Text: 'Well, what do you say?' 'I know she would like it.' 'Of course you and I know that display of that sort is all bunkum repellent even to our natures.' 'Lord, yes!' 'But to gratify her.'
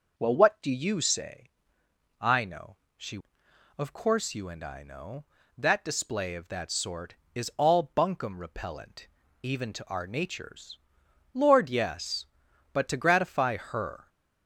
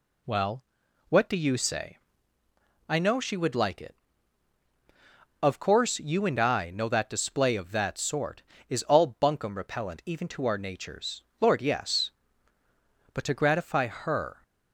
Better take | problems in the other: second | pauses between "know" and "she"; slight; at 2.7 s; 0.20 s long // skips "would like it"; at 3.4 s // pauses between "repellent" and "even"; slight; at 9.0 s; 0.34 s long

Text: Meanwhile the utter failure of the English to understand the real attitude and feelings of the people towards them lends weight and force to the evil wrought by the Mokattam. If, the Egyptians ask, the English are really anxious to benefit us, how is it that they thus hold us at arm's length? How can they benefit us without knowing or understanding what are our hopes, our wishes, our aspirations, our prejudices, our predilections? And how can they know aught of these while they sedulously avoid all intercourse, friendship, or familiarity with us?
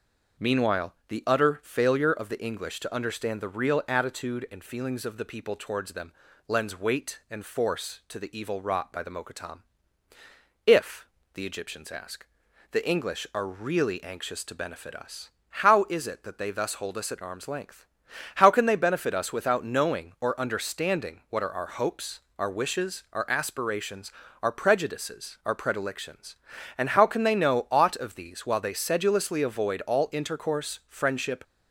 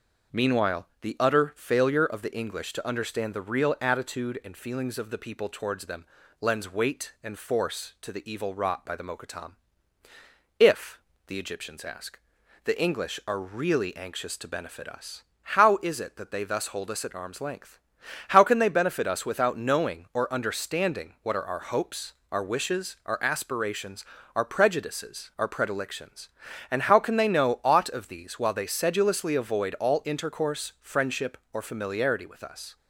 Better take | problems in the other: second | starts louder than the rest; noticeable; until 1.5 s; 6 dB; noticeable in the second // pauses between "Meanwhile" and "the"; slight; at 0.9 s; 0.16 s long; slight in the second // pauses between "them" and "lends"; slight; at 6.1 s; 0.36 s long; slight in the second // stops before "or familiarity with us"; at 31.4 s

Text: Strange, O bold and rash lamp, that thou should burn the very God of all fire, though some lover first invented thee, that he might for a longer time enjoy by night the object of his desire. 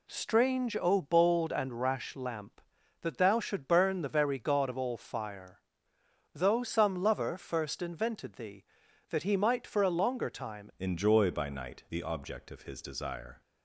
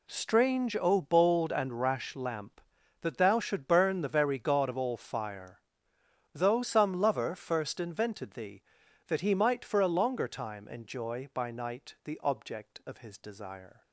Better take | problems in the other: second | changes voice at "enjoy"; from 10.7 s on; 2.7 s long

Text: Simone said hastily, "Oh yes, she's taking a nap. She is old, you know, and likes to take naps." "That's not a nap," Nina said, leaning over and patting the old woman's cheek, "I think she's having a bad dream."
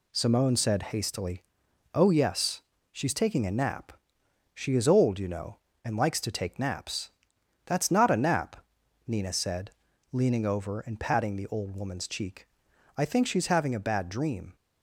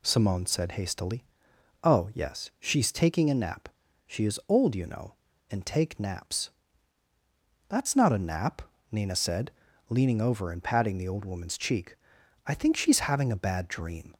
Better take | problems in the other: first | skips "likes to"; at 5.6 s

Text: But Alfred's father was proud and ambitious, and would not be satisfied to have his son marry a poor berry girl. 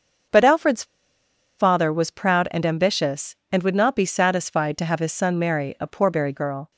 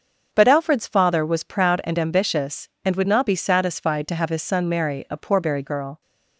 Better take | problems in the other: second | starts louder than the rest; until 2.0 s; 6.5 dB; also in the second // pauses between "Alfred's" and "father"; noticeable; at 0.8 s; 0.73 s long

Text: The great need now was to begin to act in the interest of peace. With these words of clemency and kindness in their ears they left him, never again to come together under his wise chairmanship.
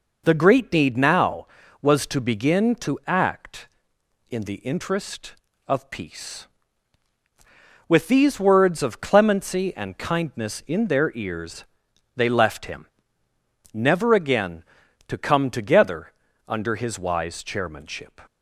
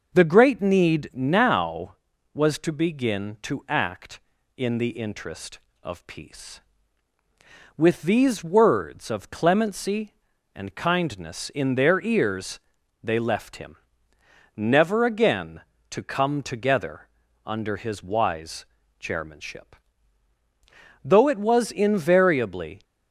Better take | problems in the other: first | pauses between "ears" and "they"; at 12.5 s; 0.44 s long; noticeable in the first // pauses between "together" and "under"; slight; at 17.0 s; 0.36 s long; also in the first // pauses between "wise" and "chairmanship"; slight; at 18.6 s; 0.34 s long // goes on to say "Though it was invariably"; strong; from 21.0 s on; 1.8 s long

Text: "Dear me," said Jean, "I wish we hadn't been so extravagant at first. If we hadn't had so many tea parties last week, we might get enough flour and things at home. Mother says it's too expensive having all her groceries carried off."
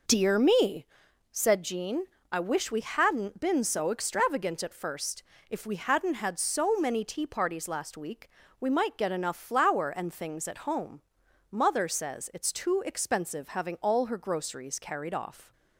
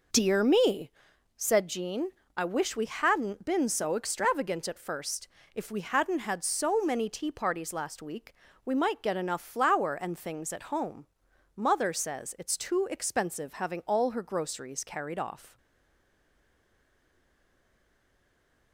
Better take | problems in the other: first | stays silent after the last word; strong; from 15.5 s on; 3.2 s long

